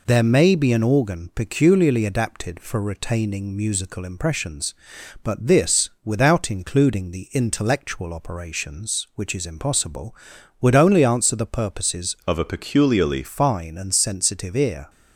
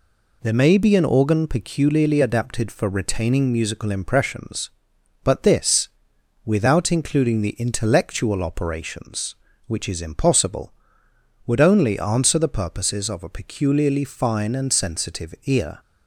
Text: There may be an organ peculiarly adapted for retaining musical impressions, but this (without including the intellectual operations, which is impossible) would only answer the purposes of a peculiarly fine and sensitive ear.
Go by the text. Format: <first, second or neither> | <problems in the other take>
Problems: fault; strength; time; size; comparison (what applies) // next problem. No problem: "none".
second | changes voice from "of" to "peculiarly"; from 12.2 to 13.2 s; 1.0 s long